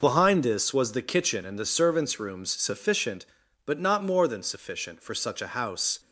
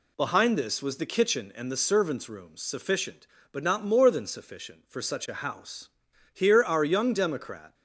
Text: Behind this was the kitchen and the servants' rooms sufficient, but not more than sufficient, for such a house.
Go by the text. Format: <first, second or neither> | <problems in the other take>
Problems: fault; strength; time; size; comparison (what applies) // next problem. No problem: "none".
first | goes on to say "Here our young democrat"; from 6.3 s on; 1.4 s long